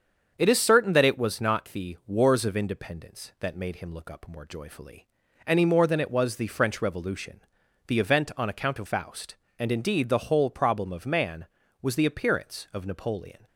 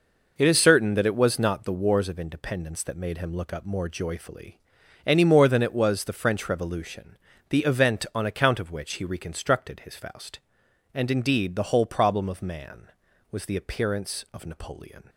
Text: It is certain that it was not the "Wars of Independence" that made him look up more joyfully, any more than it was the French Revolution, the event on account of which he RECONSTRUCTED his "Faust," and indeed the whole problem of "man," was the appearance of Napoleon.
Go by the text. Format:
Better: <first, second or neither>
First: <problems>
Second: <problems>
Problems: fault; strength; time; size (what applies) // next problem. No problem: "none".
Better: second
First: starts louder than the rest; strong; until 1.3 s; 7 dB // skips "which he RECONSTRUCTED his"; at 8.8 s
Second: none